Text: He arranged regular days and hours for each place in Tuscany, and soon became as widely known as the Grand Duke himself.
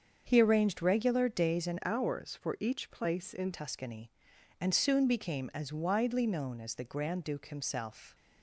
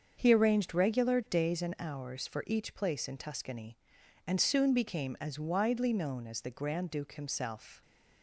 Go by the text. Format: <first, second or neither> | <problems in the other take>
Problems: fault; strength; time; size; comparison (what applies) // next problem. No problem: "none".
second | starts louder than the rest; until 1.2 s; 7 dB; also in the second // changes voice from "hours" to "in"; from 1.8 to 3.5 s; 1.7 s long